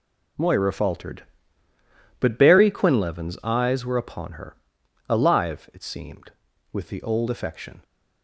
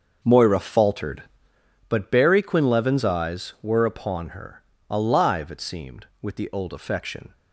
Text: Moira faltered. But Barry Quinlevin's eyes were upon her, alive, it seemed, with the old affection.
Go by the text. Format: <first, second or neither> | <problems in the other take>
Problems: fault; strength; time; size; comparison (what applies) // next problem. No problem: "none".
first | starts louder than the rest; until 1.8 s; 6.5 dB